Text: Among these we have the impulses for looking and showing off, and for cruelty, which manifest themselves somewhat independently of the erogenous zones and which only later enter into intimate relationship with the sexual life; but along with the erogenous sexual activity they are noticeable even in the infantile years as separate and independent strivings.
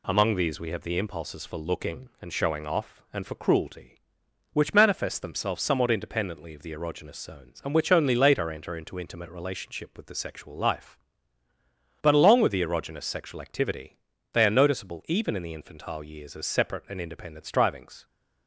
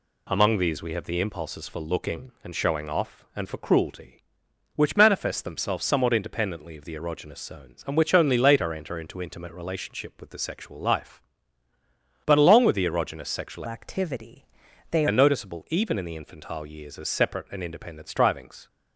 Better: first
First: pauses between "activity" and "they"; at 13.9 s; 0.38 s long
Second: changes voice from "activity" to "they"; from 13.6 to 15.0 s; 1.4 s long // pauses between "activity" and "they"; at 14.4 s; 0.44 s long

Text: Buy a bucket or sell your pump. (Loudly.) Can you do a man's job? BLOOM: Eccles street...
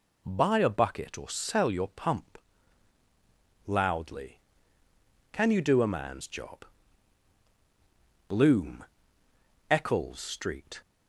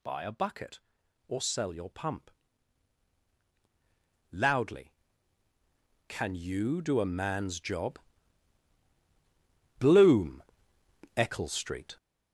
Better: first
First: none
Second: gets louder; strong; throughout; 7 dB

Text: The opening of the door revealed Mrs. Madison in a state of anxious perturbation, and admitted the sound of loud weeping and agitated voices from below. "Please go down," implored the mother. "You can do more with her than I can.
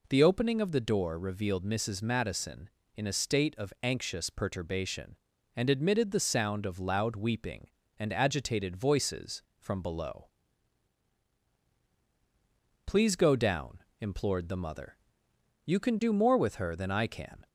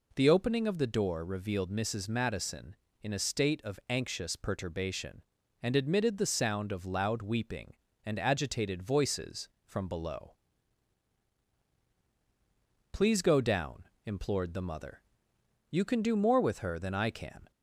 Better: neither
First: none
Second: none

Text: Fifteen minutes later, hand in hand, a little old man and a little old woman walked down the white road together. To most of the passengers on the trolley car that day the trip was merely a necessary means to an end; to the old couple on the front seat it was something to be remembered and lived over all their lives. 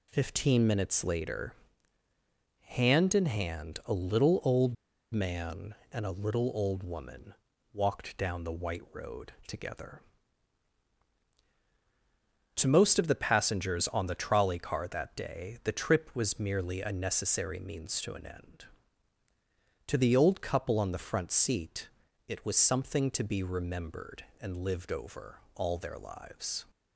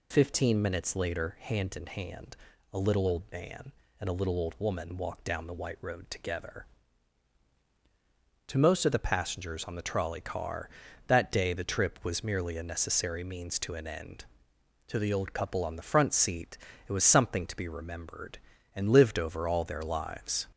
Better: second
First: pauses between "old" and "man"; at 4.7 s; 0.39 s long // pauses between "woman" and "walked"; at 7.3 s; 0.40 s long // pauses between "seat" and "it"; at 21.8 s; 0.38 s long // pauses between "over" and "all"; slight; at 25.3 s; 0.16 s long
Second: pauses between "seat" and "it"; slight; at 16.5 s; 0.32 s long

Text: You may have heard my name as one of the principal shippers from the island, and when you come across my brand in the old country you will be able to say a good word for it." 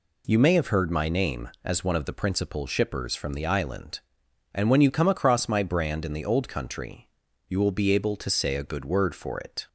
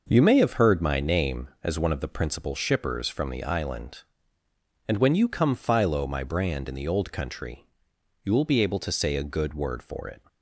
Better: first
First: pauses between "country" and "you"; at 7.0 s; 0.40 s long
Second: says "philo" for "across"; at 5.5 s // pauses between "country" and "you"; noticeable; at 7.6 s; 0.58 s long

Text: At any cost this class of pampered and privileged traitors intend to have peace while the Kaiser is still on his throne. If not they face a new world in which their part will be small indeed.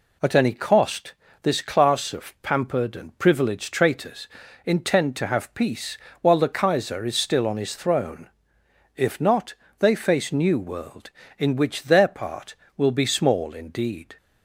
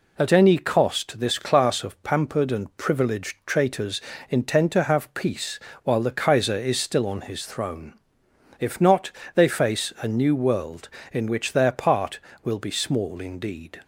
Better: second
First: pauses between "cost" and "this"; slight; at 1.1 s; 0.30 s long // pauses between "traitors" and "intend"; at 4.2 s; 0.38 s long // pauses between "peace" and "while"; slight; at 5.9 s; 0.24 s long // pauses between "not" and "they"; slight; at 9.5 s; 0.24 s long // skips "a"; at 10.3 s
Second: pauses between "traitors" and "intend"; slight; at 4.0 s; 0.26 s long // pauses between "peace" and "while"; slight; at 5.5 s; 0.26 s long // pauses between "not" and "they"; slight; at 9.0 s; 0.26 s long

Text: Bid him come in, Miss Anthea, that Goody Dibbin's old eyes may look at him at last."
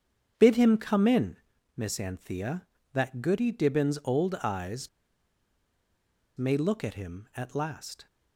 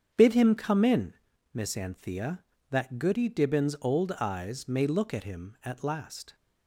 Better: second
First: starts louder than the rest; strong; until 1.3 s; 7.5 dB // pauses between "eyes" and "may"; strong; at 4.8 s; 1.4 s long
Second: starts louder than the rest; strong; until 1.5 s; 7.5 dB

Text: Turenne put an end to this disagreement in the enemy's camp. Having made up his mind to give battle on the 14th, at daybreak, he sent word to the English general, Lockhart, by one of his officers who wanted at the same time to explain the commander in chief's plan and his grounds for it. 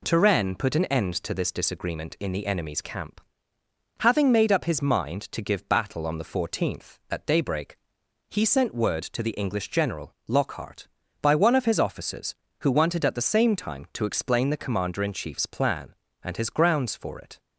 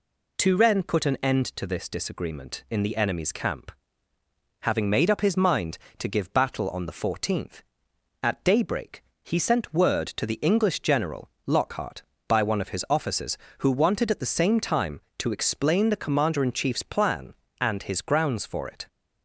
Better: neither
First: none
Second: none

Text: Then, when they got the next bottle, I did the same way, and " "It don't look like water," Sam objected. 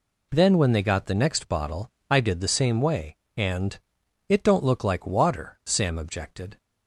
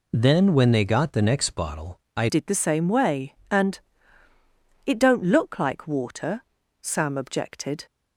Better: first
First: none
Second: changes voice at "did"; from 2.2 s on; 5.6 s long

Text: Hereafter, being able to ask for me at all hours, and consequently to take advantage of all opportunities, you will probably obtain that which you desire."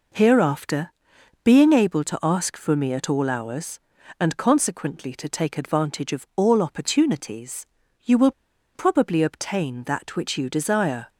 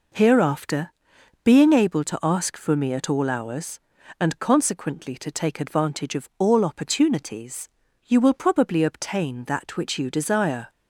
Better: second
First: pauses between "will" and "probably"; at 8.3 s; 0.44 s long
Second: none

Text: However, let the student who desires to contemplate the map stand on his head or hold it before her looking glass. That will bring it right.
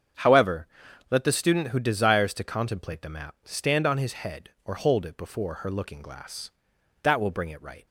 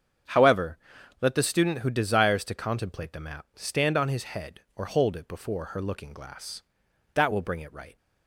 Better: neither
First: starts louder than the rest; strong; until 1.6 s; 7.5 dB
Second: starts louder than the rest; strong; until 1.7 s; 7.5 dB

